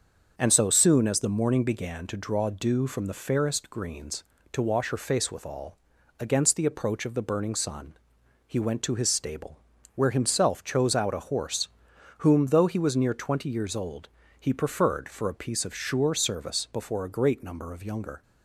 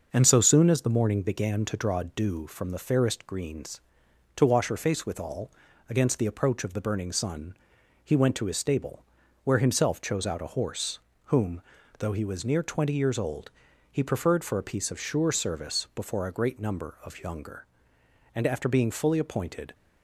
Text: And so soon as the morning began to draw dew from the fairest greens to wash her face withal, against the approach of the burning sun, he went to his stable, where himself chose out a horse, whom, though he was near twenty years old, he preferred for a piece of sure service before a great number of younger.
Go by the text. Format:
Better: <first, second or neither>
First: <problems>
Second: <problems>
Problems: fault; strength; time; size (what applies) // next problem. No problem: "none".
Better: first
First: starts louder than the rest; until 1.3 s; 6.5 dB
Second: starts louder than the rest; until 1.1 s; 6 dB // goes on to say "And after being fully appointed"; from 18.3 s on; 1.3 s long